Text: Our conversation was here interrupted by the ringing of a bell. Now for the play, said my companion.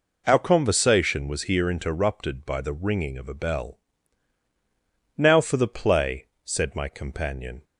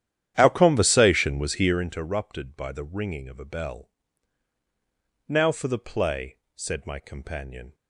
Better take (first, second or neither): first